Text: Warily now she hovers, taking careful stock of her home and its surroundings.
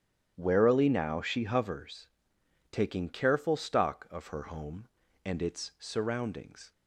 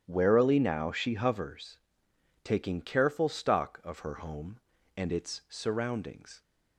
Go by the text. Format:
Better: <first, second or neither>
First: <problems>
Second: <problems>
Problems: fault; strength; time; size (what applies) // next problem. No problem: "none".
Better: neither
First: starts louder than the rest; strong; until 1.3 s; 10 dB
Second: starts louder than the rest; strong; until 1.0 s; 10 dB